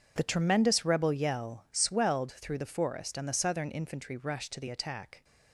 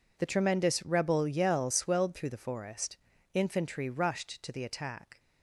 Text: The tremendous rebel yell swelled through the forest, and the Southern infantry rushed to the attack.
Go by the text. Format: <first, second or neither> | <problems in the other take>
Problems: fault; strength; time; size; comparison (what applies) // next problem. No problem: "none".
first | skips "and the Southern"; at 3.1 s